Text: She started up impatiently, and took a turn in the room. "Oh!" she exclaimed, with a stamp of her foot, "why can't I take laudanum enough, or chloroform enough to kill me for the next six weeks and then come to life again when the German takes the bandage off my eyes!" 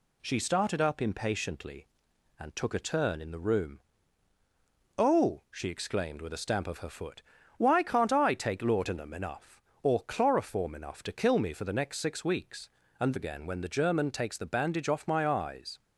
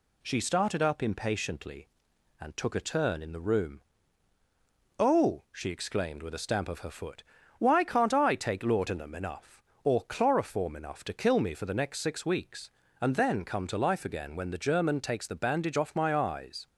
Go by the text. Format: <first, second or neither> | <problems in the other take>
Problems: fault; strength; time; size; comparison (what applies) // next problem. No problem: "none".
second | skips "then come to life"; at 13.1 s